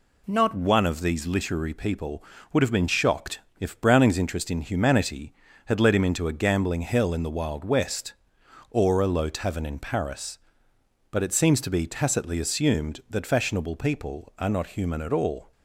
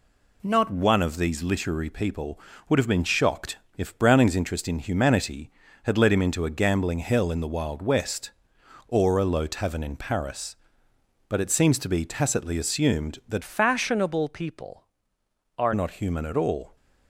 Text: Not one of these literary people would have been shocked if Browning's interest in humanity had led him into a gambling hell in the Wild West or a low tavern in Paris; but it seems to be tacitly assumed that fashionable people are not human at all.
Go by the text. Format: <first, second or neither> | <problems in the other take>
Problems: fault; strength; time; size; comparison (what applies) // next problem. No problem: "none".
first | pauses between "shocked" and "if"; slight; at 3.5 s; 0.18 s long; slight in the first // changes voice from "fashionable" to "are"; from 13.4 to 15.7 s; 2.3 s long